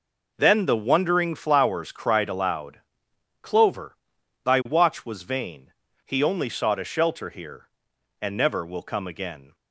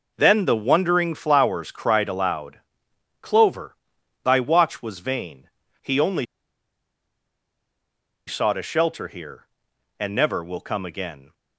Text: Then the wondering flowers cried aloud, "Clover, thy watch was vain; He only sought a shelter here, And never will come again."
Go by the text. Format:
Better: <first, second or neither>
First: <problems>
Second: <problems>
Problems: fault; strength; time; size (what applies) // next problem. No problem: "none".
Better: first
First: none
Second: pauses between "only" and "sought"; strong; at 6.2 s; 2.0 s long